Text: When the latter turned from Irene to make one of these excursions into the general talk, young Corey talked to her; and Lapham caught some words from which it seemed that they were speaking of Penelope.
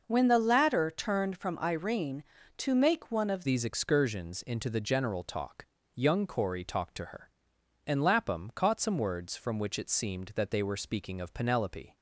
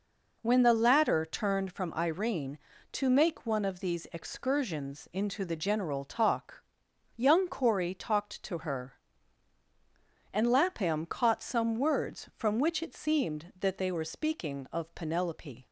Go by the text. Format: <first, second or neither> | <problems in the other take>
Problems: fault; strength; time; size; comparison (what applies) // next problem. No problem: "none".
second | changes voice at "these"; from 3.4 s on; 8.5 s long